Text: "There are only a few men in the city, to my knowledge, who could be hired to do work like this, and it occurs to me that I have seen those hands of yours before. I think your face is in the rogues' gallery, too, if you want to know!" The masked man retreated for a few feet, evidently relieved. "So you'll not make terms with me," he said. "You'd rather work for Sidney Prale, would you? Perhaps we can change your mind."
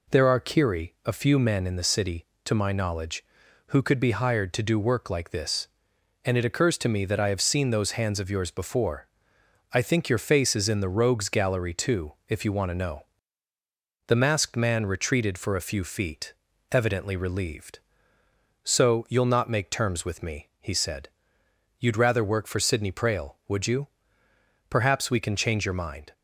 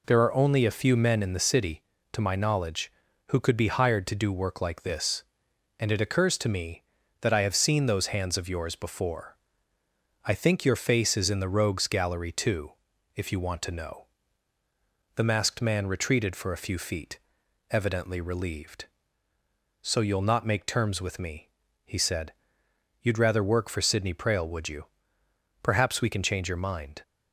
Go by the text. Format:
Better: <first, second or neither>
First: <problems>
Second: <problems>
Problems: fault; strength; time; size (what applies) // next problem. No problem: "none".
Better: second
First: says "kiri" for "only"; at 0.3 s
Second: none